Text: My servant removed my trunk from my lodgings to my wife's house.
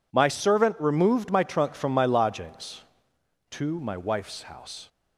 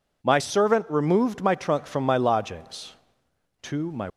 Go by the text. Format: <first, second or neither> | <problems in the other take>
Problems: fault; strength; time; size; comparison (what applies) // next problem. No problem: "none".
first | stops before "wife's house"; at 4.0 s